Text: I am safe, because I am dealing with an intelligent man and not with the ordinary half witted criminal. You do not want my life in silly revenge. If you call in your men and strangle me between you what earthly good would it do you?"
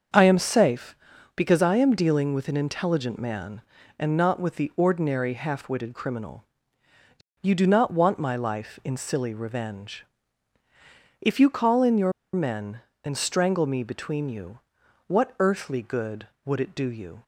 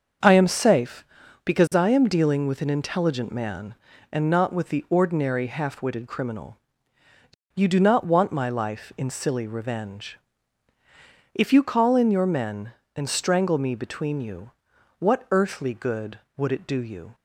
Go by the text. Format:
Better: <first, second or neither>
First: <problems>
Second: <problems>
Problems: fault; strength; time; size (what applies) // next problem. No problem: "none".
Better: second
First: starts louder than the rest; until 1.5 s; 7 dB // pauses between "your" and "men"; slight; at 12.1 s; 0.21 s long // pauses between "you" and "what"; noticeable; at 14.5 s; 0.48 s long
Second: starts louder than the rest; until 1.6 s; 7 dB // pauses between "you" and "what"; noticeable; at 14.5 s; 0.48 s long